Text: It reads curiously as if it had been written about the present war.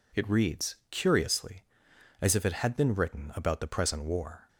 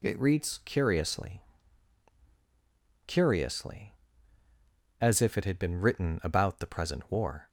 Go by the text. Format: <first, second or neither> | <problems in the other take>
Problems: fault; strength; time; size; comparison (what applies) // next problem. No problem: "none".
first | says "curiously" twice; at 3.0 s